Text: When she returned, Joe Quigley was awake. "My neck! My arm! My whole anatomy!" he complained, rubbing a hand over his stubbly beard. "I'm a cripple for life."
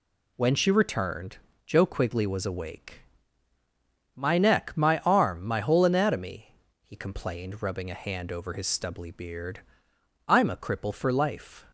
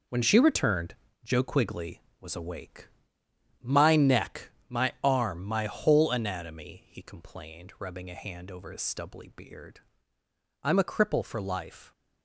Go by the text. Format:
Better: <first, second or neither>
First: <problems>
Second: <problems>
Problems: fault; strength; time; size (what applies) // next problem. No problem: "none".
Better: first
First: none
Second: gets quieter; strong; throughout; 9 dB